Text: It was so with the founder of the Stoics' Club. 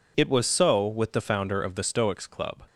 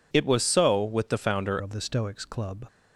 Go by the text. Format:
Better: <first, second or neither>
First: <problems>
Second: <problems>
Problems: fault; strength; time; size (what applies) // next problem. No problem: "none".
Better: first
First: none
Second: changes voice at "of"; from 1.6 s on; 1.0 s long